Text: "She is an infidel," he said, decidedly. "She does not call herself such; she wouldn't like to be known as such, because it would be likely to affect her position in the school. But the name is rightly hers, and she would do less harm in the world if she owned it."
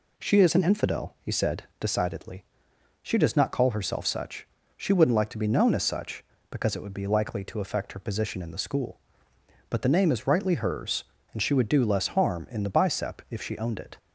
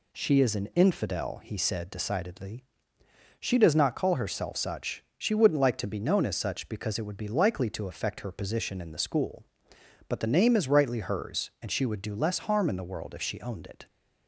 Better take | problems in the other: second | says "bicep" for "world"; at 12.6 s

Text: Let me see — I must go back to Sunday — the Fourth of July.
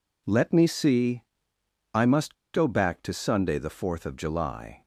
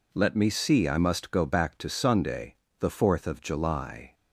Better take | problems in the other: second | pauses between "must" and "go"; slight; at 2.3 s; 0.19 s long

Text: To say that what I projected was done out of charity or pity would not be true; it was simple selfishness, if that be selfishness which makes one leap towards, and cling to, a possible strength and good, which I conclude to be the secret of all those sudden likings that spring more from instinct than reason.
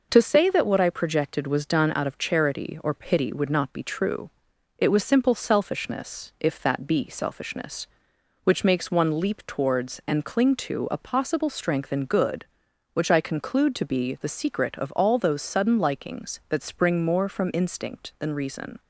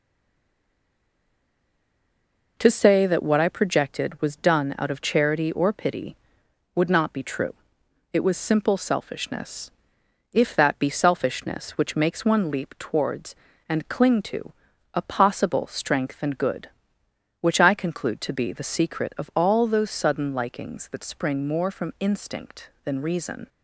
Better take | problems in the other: first | stays silent before the first word; strong; until 2.5 s; 2.5 s long

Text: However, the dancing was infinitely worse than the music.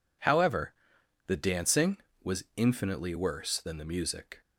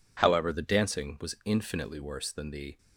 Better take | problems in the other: first | stops before "music"; at 2.7 s

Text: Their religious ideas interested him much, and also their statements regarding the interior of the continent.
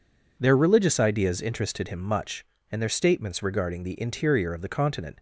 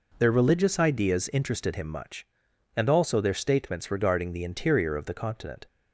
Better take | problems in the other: second | skips "also"; at 2.7 s

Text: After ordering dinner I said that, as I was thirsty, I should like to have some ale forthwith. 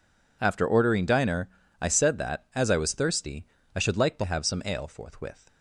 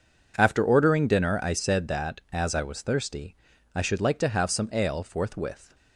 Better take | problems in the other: second | says "diner" for "dinner"; at 1.0 s

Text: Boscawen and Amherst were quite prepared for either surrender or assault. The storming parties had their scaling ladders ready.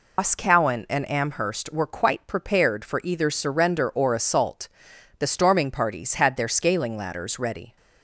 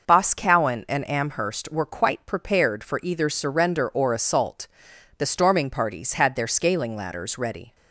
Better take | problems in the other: second | loses the start of "Boscawen"; at 0.1 s; 105 ms

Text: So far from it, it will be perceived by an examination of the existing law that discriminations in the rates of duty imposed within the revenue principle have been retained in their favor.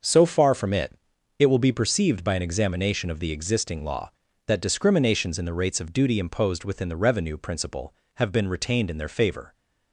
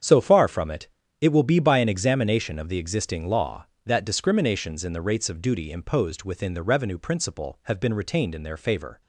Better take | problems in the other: first | starts louder than the rest; strong; until 1.3 s; 8 dB; also in the first // skips "perceived"; at 1.5 s

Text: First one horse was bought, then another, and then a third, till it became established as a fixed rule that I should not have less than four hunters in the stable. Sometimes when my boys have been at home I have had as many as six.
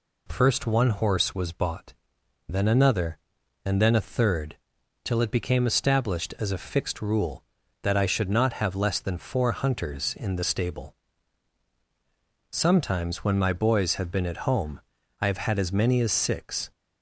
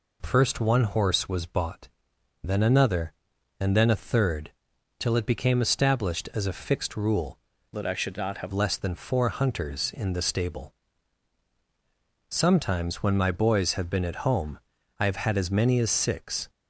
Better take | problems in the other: first | changes voice from "that" to "have"; from 7.7 to 8.5 s; 0.8 s long // pauses between "home" and "I"; at 14.5 s; 0.40 s long; also in the first

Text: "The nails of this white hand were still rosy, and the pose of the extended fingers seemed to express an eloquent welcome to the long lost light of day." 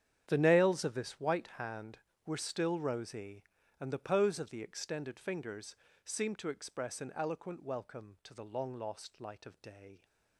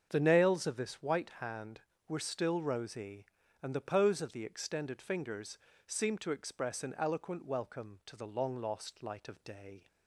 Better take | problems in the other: second | gets quieter; strong; throughout; 16.5 dB // starts louder than the rest; strong; until 1.2 s; 9.5 dB; also in the second // pauses between "fingers" and "seemed"; slight; at 5.7 s; 0.26 s long; slight in the second

